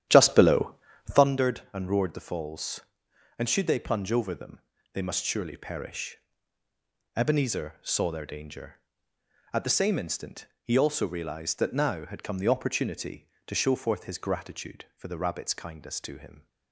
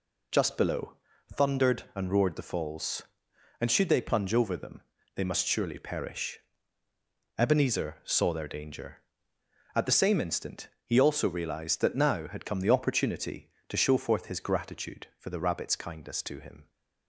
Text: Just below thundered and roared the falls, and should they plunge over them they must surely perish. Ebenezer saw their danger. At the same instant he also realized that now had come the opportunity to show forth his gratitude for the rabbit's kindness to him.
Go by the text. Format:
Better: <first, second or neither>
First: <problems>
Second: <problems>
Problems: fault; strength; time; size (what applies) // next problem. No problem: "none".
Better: second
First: starts louder than the rest; strong; until 1.4 s; 11 dB // pauses between "below" and "thundered"; at 0.7 s; 0.38 s long // pauses between "them" and "they"; slight; at 4.5 s; 0.32 s long // pauses between "instant" and "he"; slight; at 10.4 s; 0.16 s long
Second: pauses between "below" and "thundered"; at 0.9 s; 0.38 s long // pauses between "them" and "they"; slight; at 4.8 s; 0.32 s long // pauses between "instant" and "he"; slight; at 10.6 s; 0.16 s long